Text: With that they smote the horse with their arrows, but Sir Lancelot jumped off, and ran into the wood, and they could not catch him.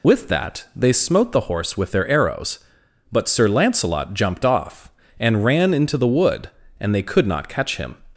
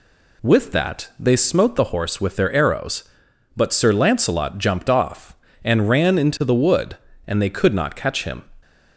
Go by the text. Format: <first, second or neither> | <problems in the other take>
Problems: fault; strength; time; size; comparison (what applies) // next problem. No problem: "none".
second | loses the start of "With"; at 0.0 s; 90 ms